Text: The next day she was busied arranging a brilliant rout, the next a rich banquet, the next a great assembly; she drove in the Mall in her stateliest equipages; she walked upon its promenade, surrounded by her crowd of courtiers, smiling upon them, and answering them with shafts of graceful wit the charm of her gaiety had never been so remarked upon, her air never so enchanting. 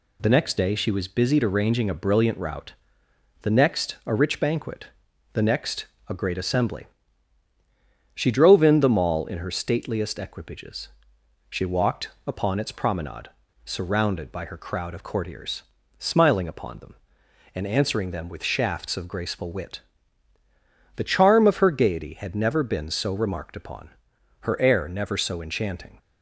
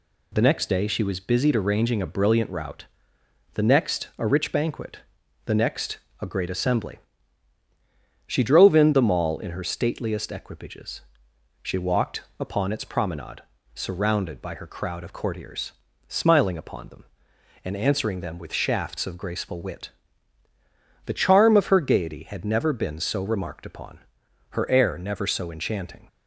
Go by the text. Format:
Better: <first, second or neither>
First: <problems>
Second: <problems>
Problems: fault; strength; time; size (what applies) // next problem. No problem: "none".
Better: neither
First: pauses between "next" and "a"; slight; at 5.8 s; 0.22 s long // pauses between "walked" and "upon"; slight; at 12.1 s; 0.16 s long // pauses between "wit" and "the"; at 19.7 s; 1.1 s long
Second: pauses between "next" and "a"; slight; at 5.9 s; 0.22 s long // pauses between "walked" and "upon"; slight; at 12.2 s; 0.16 s long // pauses between "wit" and "the"; at 19.8 s; 1.1 s long